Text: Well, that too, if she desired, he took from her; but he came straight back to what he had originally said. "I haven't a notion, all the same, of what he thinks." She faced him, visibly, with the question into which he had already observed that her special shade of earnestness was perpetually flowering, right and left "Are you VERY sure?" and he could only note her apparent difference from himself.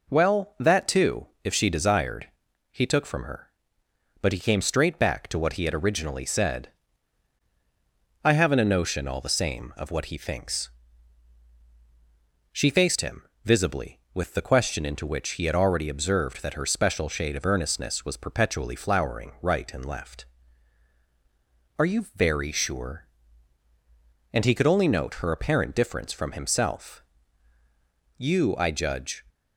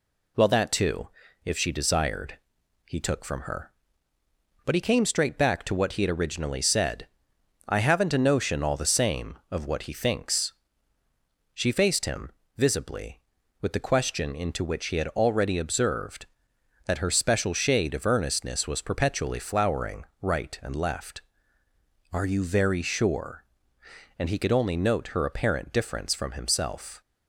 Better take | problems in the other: second | goes on to say "You I judge"; noticeable; from 28.1 s on; 1.0 s long

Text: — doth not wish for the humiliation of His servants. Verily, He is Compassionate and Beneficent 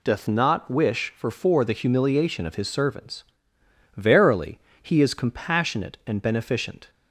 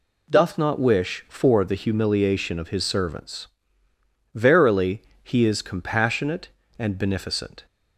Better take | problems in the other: second | says "for" twice; at 1.2 s

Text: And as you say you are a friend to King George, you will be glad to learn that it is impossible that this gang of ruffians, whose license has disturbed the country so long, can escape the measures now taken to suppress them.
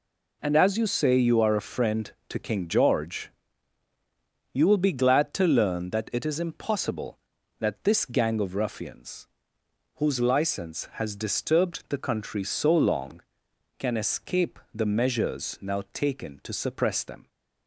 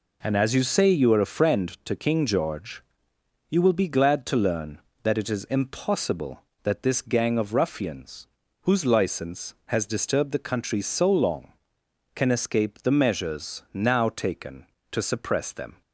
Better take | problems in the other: neither | none

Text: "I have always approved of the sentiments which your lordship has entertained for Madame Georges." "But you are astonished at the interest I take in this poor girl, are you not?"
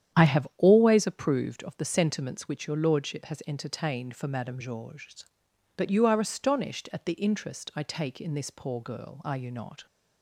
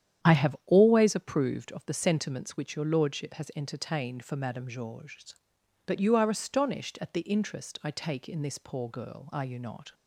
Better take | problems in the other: neither | starts louder than the rest; strong; the same in both

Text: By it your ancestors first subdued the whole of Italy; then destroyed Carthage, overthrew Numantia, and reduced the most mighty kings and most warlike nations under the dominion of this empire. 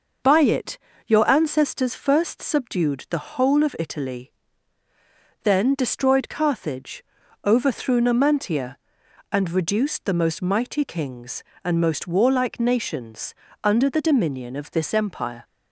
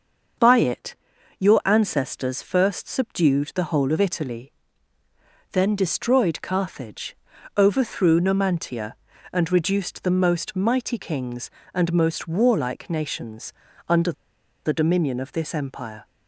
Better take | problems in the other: first | starts louder than the rest; until 1.8 s; 6.5 dB // pauses between "it" and "your"; noticeable; at 0.9 s; 0.46 s long; slight in the first // pauses between "nations" and "under"; slight; at 13.5 s; 0.36 s long; slight in the first // pauses between "under" and "the"; noticeable; at 14.1 s; 0.52 s long

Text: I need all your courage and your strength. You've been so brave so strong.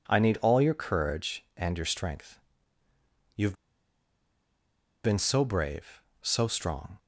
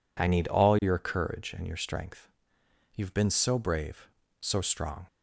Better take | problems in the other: second | pauses between "You've" and "been"; strong; at 3.5 s; 1.4 s long

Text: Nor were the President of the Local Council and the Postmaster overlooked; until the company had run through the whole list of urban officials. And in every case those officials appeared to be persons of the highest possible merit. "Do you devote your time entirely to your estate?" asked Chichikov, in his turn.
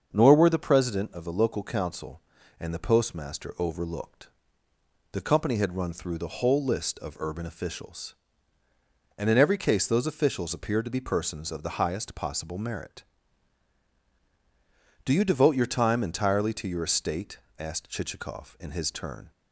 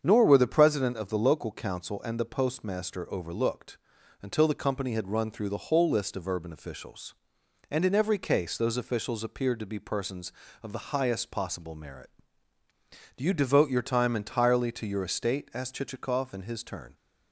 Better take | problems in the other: second | starts louder than the rest; until 1.1 s; 6.5 dB; strong in the second // skips "until"; at 4.7 s

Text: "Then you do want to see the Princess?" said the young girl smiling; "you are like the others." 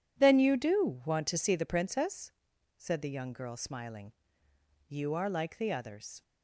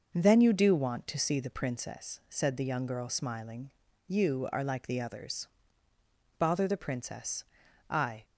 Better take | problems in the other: first | goes on to say "Bother the Princess I"; strong; from 6.3 s on; 1.8 s long

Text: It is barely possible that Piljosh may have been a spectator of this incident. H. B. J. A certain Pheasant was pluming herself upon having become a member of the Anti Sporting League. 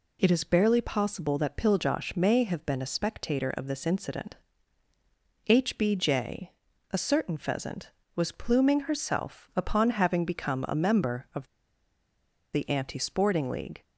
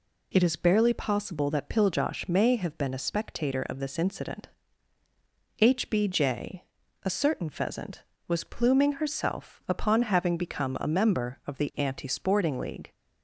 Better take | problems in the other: second | pauses between "J" and "A"; at 6.5 s; 0.40 s long; also in the second // pauses between "of" and "the"; at 11.4 s; 1.0 s long

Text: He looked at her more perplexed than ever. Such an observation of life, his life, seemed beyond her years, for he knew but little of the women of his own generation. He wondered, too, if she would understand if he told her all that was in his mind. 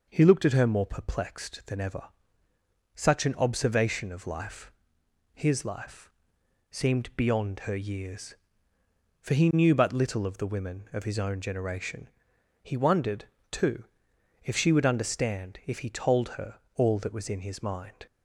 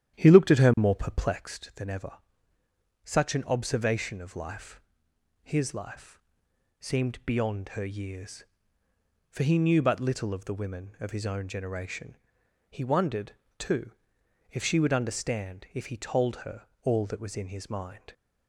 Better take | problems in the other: first | starts louder than the rest; strong; until 1.6 s; 10.5 dB // pauses between "her" and "all"; slight; at 16.6 s; 0.18 s long; slight in the first

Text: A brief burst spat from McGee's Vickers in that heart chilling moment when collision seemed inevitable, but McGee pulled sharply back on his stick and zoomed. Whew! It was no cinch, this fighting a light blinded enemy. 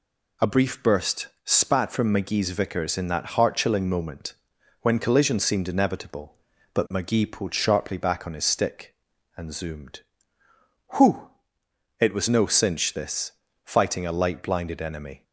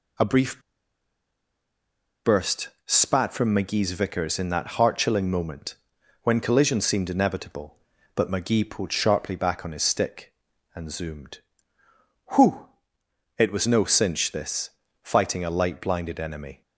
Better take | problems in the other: first | pauses between "brief" and "burst"; strong; at 0.6 s; 1.6 s long // pauses between "burst" and "spat"; slight; at 2.6 s; 0.18 s long; slight in the first // pauses between "moment" and "when"; noticeable; at 5.7 s; 0.48 s long; noticeable in the first // pauses between "this" and "fighting"; slight; at 14.7 s; 0.32 s long; slight in the first

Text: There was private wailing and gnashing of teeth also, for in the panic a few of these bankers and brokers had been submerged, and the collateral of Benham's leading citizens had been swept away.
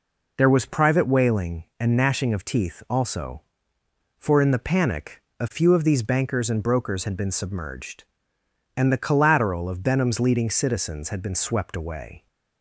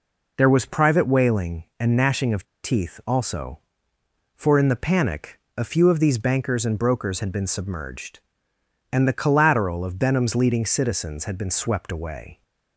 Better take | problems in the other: first | pauses between "of" and "teeth"; slight; at 2.4 s; 0.20 s long // pauses between "panic" and "a"; slight; at 5.3 s; 0.18 s long; slight in the first

